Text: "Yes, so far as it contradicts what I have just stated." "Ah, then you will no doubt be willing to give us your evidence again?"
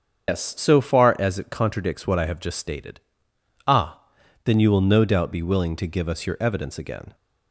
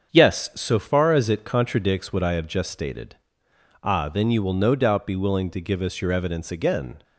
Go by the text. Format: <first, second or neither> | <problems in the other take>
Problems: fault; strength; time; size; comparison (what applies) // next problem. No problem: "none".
second | loses the start of "Yes"; at 0.2 s; 135 ms // starts louder than the rest; strong; until 1.3 s; 7 dB; strong in the second